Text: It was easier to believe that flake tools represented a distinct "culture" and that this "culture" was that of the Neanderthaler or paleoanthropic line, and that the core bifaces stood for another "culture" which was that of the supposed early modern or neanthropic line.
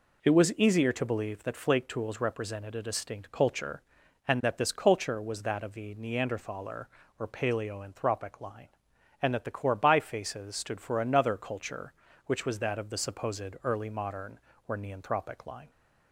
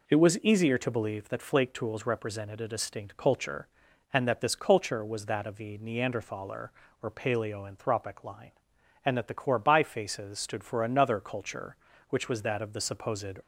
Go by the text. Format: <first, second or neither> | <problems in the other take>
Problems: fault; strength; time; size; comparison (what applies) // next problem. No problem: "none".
first | stops before "early modern or neanthropic line"; at 13.4 s